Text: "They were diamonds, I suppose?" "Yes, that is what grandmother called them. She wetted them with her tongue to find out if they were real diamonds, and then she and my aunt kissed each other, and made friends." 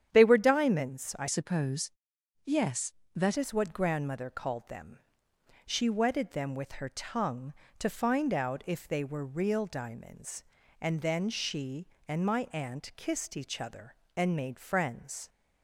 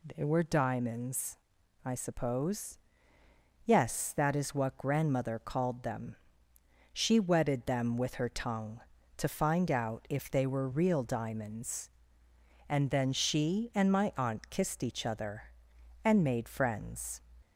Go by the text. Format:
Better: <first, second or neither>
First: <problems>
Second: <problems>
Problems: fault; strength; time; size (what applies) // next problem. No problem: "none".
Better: second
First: starts louder than the rest; strong; until 1.1 s; 9.5 dB // changes voice from "suppose" to "that"; from 1.2 to 3.3 s; 2.1 s long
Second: none